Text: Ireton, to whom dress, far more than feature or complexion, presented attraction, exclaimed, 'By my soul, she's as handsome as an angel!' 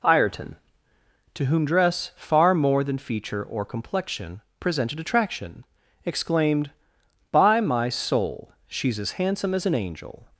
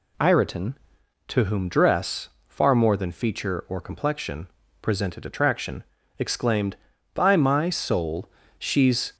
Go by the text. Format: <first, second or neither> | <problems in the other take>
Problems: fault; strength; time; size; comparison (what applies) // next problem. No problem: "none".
first | stops before "as handsome as an angel"; at 9.1 s